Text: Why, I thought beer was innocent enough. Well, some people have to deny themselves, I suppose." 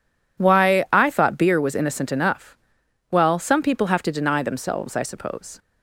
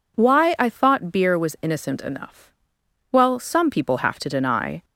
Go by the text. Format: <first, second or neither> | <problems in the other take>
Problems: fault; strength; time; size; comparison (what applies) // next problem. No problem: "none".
first | stops before "themselves I suppose"; at 4.8 s